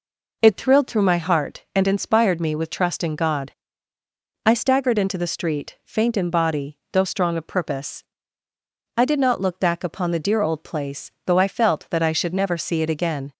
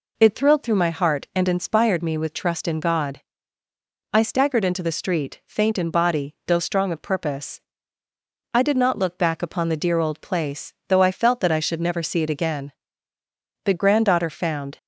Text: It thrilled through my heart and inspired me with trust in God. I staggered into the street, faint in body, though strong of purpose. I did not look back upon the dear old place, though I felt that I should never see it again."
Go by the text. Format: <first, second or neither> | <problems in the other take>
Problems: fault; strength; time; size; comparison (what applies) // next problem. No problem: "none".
first | goes on to say "The granddaughter found"; noticeable; from 13.6 s on; 1.1 s long